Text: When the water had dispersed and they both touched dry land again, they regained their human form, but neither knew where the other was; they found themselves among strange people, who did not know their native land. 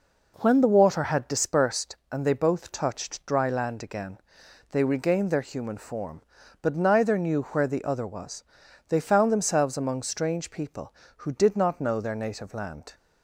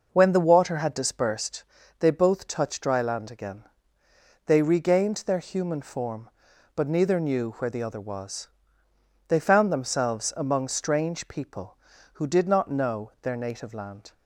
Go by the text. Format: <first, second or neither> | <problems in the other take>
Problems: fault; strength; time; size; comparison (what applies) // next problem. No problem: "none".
first | skips "and"; at 1.8 s